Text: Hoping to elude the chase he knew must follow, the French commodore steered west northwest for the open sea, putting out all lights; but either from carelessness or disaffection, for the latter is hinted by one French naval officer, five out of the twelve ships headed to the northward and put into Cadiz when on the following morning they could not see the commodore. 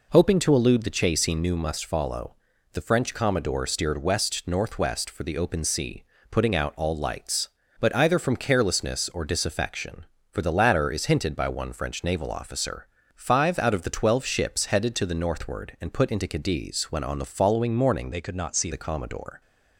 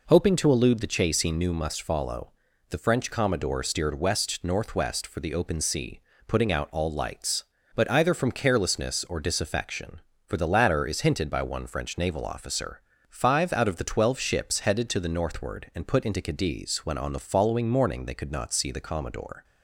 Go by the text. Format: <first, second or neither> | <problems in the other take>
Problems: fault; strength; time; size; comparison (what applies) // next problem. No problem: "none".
second | changes voice from "they" to "see"; from 18.1 to 18.6 s; 0.5 s long